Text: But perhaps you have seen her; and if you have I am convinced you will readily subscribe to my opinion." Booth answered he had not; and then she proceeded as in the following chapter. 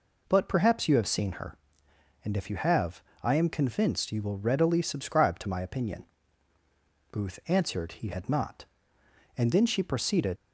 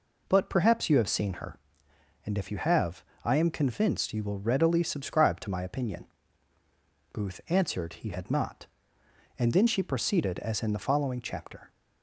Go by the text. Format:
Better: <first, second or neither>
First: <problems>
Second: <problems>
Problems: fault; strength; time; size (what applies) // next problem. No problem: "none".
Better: second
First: pauses between "have" and "I"; slight; at 3.0 s; 0.20 s long // stops before "as in the following chapter"; at 10.3 s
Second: pauses between "have" and "I"; slight; at 3.0 s; 0.20 s long